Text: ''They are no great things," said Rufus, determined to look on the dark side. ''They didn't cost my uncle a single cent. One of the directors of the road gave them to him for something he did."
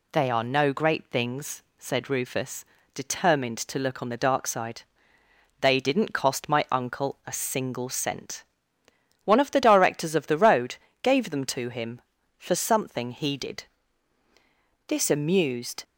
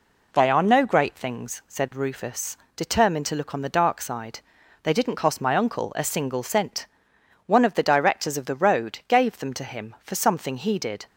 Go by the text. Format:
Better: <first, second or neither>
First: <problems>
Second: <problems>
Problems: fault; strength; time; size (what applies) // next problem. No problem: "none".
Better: second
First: pauses between "road" and "gave"; slight; at 10.7 s; 0.26 s long // goes on to say "This amused"; noticeable; from 14.8 s on; 0.96 s long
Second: none